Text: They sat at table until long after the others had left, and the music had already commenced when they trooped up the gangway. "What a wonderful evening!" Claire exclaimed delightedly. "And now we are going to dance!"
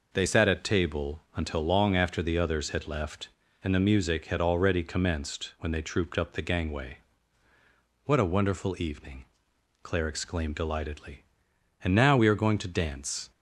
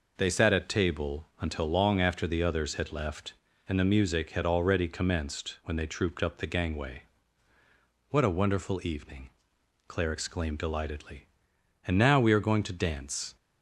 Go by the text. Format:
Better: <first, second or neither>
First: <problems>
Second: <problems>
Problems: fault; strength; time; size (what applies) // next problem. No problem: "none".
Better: neither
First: none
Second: none